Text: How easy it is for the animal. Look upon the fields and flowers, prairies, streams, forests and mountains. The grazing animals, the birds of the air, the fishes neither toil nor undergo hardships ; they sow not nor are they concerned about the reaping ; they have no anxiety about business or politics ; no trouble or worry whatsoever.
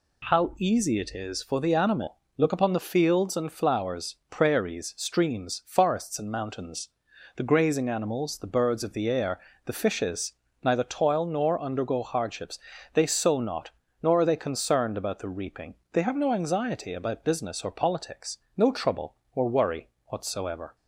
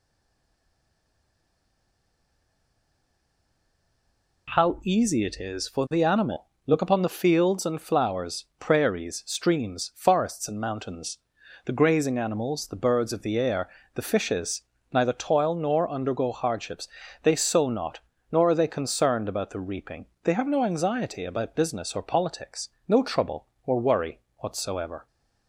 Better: first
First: pauses between "fishes" and "neither"; slight; at 10.3 s; 0.32 s long // pauses between "not" and "nor"; slight; at 13.7 s; 0.30 s long // pauses between "worry" and "whatsoever"; slight; at 19.8 s; 0.20 s long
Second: stays silent before the first word; strong; until 4.4 s; 4.4 s long // pauses between "fishes" and "neither"; slight; at 14.6 s; 0.32 s long // pauses between "not" and "nor"; slight; at 18.0 s; 0.30 s long // pauses between "worry" and "whatsoever"; slight; at 24.2 s; 0.20 s long

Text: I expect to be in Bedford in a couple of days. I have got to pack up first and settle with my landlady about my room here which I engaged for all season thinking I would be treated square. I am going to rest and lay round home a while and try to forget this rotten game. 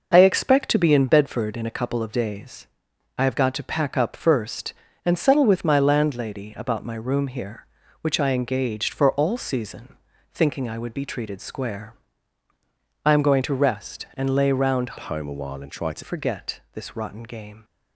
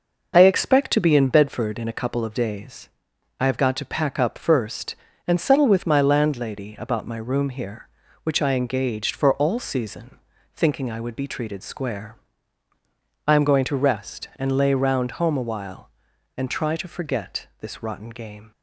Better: second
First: pauses between "season" and "thinking"; slight; at 9.9 s; 0.36 s long // changes voice from "home" to "to"; from 14.9 to 16.0 s; 1.1 s long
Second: pauses between "season" and "thinking"; slight; at 10.1 s; 0.36 s long

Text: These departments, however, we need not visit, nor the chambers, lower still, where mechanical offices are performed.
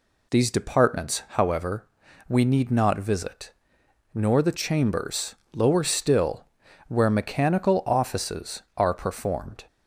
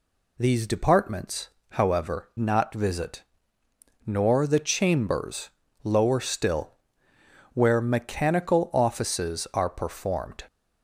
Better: first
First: none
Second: skips "we need"; at 2.3 s

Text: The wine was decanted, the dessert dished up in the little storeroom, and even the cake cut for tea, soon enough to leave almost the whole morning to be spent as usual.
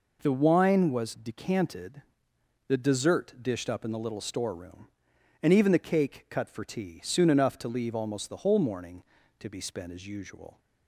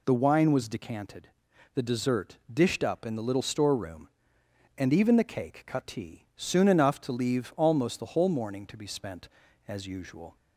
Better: first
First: none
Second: pauses between "dessert" and "dished"; slight; at 2.3 s; 0.16 s long // skips "for"; at 5.8 s

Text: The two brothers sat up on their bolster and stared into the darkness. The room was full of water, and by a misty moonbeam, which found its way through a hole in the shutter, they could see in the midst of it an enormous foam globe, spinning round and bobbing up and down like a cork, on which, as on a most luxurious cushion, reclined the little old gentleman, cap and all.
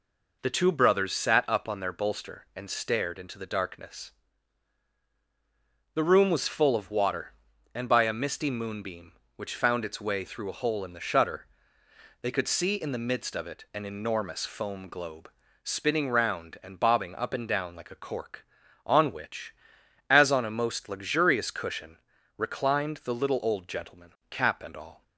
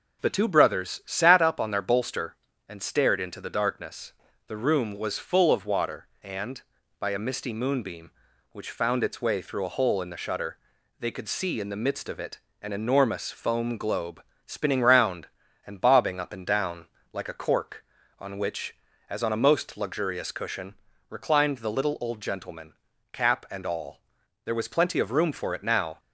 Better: first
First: none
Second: pauses between "it" and "an"; slight; at 12.3 s; 0.22 s long // pauses between "down" and "like"; slight; at 16.8 s; 0.26 s long // goes on to say "There was plenty of room for it now"; from 24.4 s on; 1.5 s long

